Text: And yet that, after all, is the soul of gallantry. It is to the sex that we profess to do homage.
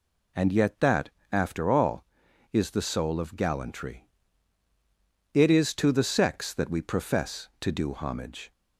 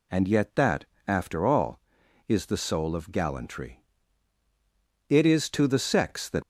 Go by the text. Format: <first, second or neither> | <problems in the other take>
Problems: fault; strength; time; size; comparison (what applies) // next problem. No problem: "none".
first | stops before "we profess to do homage"; at 6.4 s